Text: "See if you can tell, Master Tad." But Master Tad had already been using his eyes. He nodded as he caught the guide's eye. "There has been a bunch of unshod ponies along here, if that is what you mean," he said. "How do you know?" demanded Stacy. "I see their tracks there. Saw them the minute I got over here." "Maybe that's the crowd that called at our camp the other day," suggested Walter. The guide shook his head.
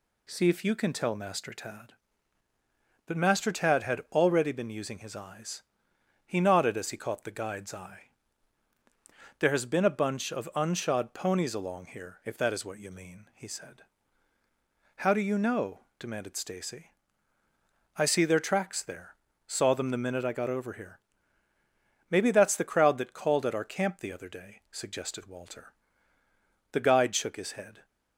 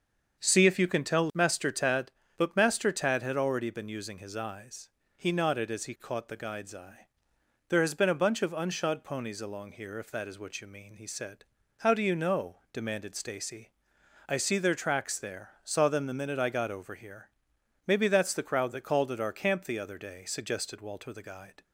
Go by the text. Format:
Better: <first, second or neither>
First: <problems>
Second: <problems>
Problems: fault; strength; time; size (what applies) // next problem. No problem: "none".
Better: first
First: none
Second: starts louder than the rest; until 1.4 s; 6.5 dB // stops before "shook his head"; at 21.6 s